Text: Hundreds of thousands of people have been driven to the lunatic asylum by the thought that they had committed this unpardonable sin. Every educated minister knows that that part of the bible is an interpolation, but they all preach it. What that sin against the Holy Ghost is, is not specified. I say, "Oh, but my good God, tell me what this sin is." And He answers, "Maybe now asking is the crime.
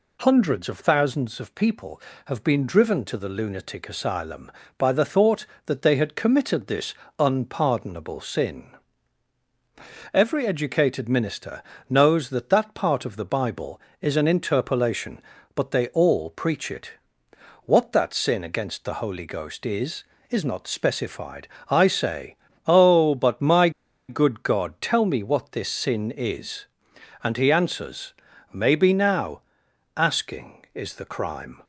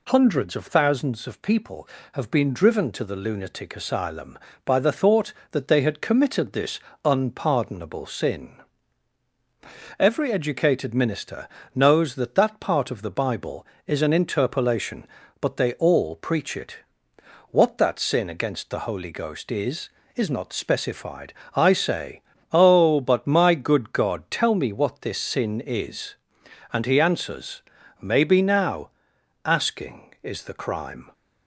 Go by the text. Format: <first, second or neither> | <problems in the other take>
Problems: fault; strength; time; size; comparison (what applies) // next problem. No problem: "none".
second | pauses between "this" and "unpardonable"; slight; at 6.9 s; 0.24 s long; slight in the second // pauses between "minister" and "knows"; slight; at 11.6 s; 0.26 s long; slight in the second // pauses between "my" and "good"; at 23.6 s; 0.39 s long // pauses between "now" and "asking"; noticeable; at 29.3 s; 0.56 s long; noticeable in the second